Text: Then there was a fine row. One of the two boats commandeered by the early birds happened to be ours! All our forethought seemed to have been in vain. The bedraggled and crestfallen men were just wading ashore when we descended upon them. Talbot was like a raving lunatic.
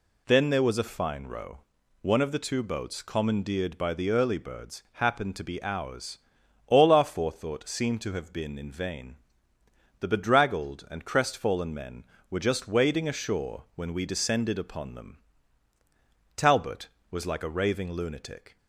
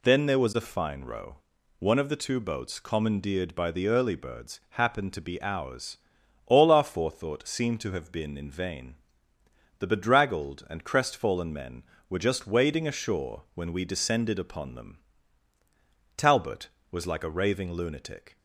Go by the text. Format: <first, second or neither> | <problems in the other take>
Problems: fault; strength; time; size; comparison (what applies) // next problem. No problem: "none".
neither | none